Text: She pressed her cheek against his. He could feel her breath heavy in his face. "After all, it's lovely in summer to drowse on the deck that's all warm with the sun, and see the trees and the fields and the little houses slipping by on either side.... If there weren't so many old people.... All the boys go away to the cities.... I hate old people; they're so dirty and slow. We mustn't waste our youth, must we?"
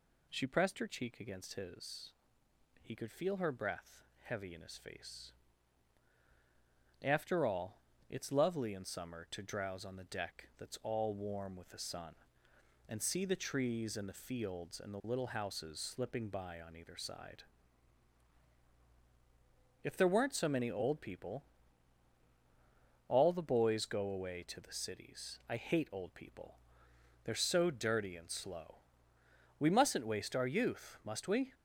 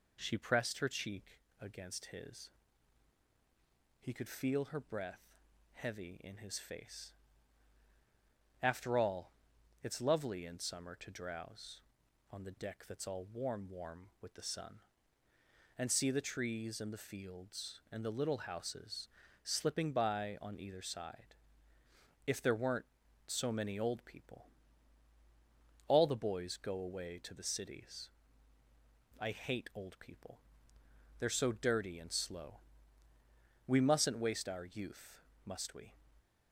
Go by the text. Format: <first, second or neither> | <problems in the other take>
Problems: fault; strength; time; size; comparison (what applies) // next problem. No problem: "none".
first | pauses between "cheek" and "against"; slight; at 1.3 s; 0.22 s long // pauses between "breath" and "heavy"; noticeable; at 5.2 s; 0.50 s long; slight in the first // says "warm" twice; at 13.6 s // pauses between "houses" and "slipping"; slight; at 19.0 s; 0.34 s long